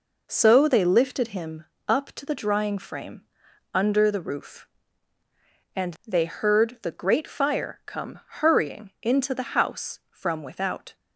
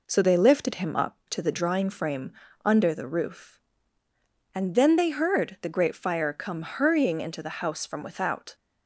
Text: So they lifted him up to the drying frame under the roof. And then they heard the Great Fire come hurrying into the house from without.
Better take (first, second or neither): second